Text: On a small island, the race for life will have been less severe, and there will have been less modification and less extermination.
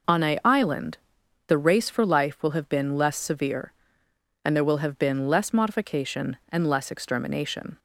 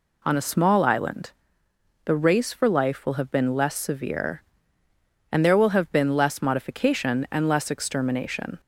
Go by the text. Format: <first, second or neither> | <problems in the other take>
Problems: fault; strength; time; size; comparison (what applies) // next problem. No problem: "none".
second | skips "small"; at 0.4 s